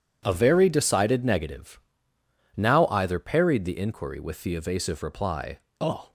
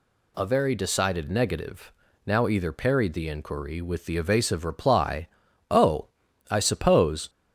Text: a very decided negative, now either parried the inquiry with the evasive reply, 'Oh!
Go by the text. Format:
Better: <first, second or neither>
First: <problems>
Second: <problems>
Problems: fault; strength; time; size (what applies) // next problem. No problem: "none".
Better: first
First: none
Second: goes on to say "I suppose"; noticeable; from 6.4 s on; 0.80 s long